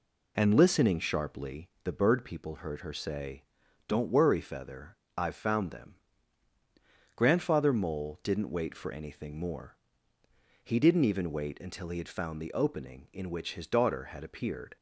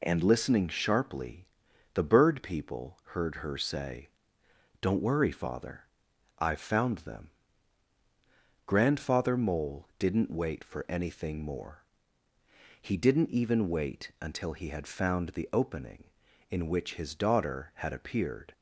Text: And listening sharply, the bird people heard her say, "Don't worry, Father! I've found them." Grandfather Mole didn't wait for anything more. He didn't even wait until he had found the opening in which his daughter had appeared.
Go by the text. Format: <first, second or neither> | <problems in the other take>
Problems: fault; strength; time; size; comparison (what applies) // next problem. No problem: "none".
second | says "Feather" for "Father"; at 4.4 s